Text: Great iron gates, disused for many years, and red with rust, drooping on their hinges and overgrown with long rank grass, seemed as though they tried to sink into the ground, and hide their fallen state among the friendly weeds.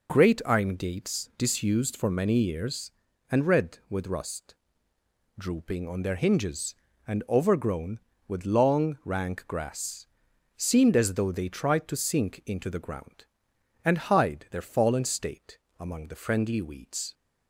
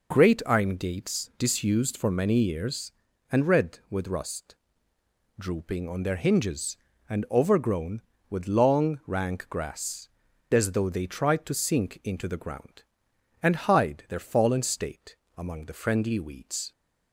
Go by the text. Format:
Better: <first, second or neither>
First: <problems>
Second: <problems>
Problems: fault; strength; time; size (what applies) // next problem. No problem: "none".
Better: first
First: pauses between "state" and "among"; slight; at 15.5 s; 0.18 s long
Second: skips "seemed"; at 10.3 s // pauses between "state" and "among"; slight; at 15.1 s; 0.18 s long